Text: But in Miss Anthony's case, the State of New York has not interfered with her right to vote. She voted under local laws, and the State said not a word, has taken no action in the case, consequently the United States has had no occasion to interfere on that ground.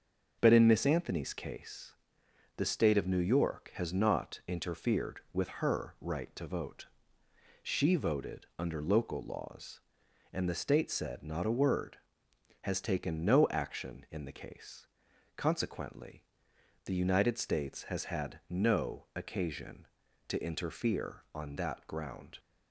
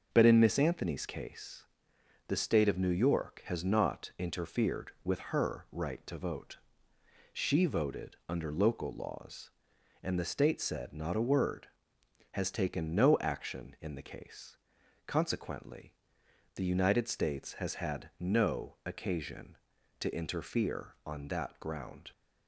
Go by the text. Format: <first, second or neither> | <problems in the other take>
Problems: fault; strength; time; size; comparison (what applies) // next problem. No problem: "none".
neither | starts louder than the rest; the same in both // pauses between "consequently" and "the"; noticeable; the same in both